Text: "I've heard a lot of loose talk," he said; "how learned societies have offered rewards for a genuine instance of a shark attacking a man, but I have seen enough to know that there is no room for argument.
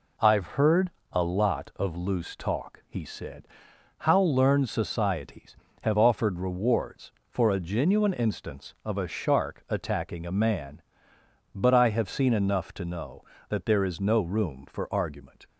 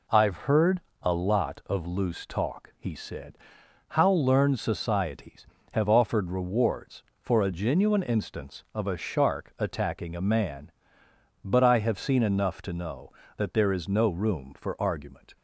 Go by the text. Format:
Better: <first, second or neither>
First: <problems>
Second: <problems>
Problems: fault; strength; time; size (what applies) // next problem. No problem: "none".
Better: neither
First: pauses between "heard" and "a"; slight; at 0.8 s; 0.22 s long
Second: pauses between "heard" and "a"; slight; at 0.7 s; 0.22 s long